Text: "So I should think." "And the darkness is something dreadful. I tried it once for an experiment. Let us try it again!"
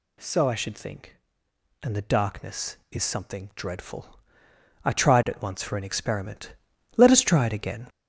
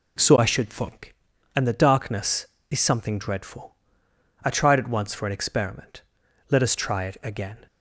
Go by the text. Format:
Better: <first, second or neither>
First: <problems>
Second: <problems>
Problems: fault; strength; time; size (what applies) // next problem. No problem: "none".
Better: second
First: gets louder; noticeable; throughout; 5.5 dB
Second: none